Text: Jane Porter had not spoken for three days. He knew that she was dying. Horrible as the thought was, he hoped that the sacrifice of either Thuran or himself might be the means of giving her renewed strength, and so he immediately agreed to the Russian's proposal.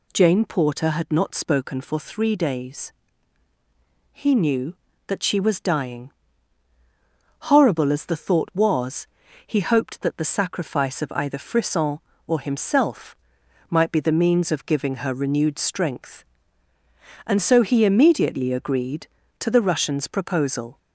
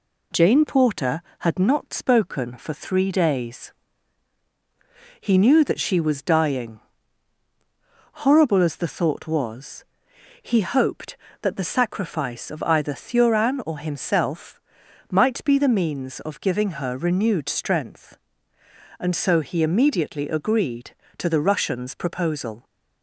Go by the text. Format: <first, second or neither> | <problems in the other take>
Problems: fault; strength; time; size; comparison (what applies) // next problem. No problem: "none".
second | says "Frisson" for "Thuran"; at 11.3 s // pauses between "himself" and "might"; noticeable; at 13.1 s; 0.54 s long; noticeable in the second